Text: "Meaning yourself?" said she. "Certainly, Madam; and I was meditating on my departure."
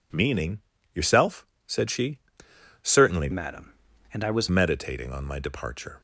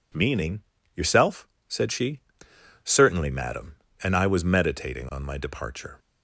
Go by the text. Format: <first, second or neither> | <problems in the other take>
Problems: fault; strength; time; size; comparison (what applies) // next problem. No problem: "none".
second | pauses between "Meaning" and "yourself"; slight; at 0.5 s; 0.34 s long; slight in the second // changes voice from "Madam" to "was"; from 3.3 to 4.4 s; 1.1 s long